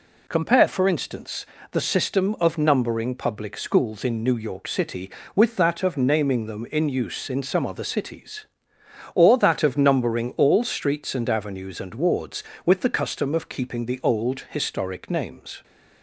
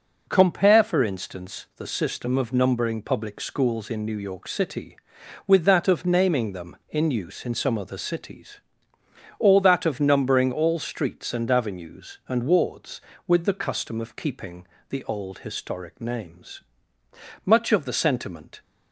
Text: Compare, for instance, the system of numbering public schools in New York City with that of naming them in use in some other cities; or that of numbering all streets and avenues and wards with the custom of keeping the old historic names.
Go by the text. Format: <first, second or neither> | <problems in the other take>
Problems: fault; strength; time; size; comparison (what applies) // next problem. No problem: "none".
first | pauses between "keeping" and "the"; slight; at 14.6 s; 0.24 s long // goes on to say "Much of the sentiment"; noticeable; from 17.4 s on; 1.1 s long